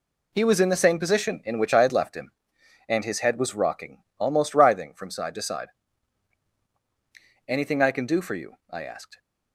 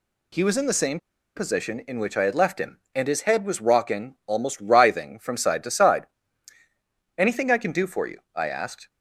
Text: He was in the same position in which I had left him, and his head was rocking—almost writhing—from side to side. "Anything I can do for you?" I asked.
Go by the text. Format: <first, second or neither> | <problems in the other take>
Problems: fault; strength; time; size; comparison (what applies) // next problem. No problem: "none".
first | pauses between "same" and "position"; at 0.9 s; 0.38 s long